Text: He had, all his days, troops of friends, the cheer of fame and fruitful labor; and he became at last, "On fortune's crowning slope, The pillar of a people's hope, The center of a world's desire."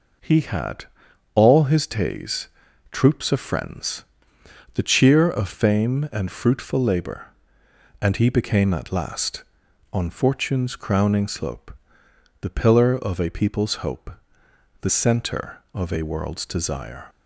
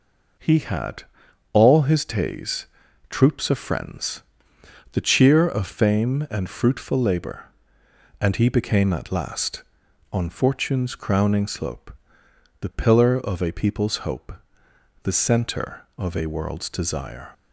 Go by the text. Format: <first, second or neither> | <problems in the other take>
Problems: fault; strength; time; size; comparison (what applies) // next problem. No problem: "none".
neither | none